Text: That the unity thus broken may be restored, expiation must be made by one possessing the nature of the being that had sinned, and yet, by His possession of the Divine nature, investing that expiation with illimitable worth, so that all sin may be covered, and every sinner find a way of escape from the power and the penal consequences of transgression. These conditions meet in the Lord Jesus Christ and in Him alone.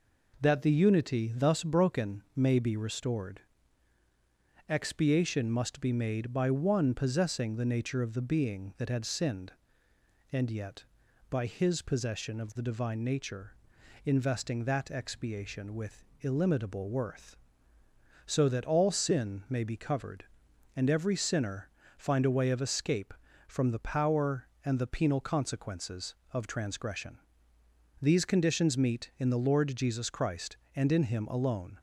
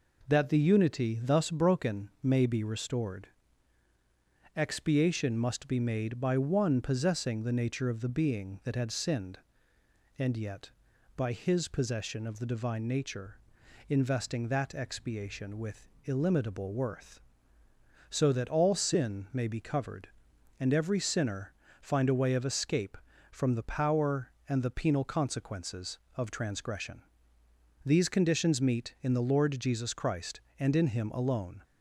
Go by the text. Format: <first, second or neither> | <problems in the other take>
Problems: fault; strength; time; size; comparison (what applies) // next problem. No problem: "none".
neither | pauses between "with" and "illimitable"; slight; the same in both // pauses between "sinner" and "find"; slight; the same in both